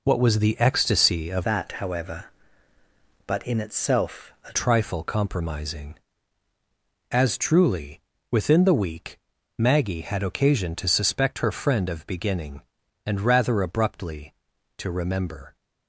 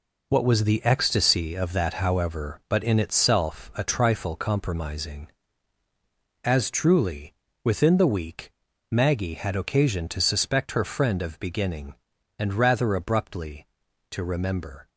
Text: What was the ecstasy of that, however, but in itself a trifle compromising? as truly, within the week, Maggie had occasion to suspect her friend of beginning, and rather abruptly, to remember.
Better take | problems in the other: second | changes voice from "that" to "a"; from 1.4 to 4.5 s; 3.1 s long // pauses between "itself" and "a"; slight; at 4.3 s; 0.16 s long

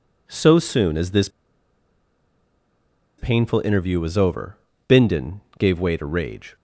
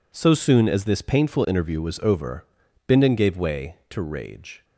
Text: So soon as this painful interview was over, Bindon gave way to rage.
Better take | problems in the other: second | pauses between "this" and "painful"; strong; at 1.2 s; 1.9 s long // pauses between "Bindon" and "gave"; slight; at 5.4 s; 0.16 s long

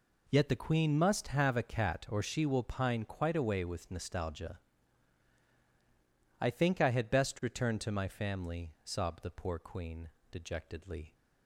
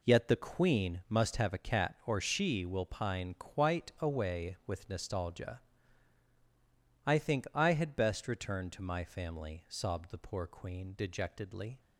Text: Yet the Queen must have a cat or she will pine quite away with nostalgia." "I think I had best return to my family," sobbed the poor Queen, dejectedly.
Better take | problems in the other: neither | none

